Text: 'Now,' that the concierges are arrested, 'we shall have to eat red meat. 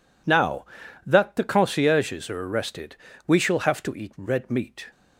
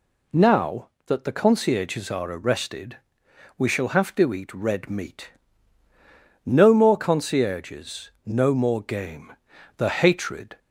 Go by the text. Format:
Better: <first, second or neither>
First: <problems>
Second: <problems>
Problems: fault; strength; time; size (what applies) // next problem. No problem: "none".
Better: first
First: none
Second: goes on to say "No more concierges no more game The hatred"; strong; from 6.4 s on; 4.1 s long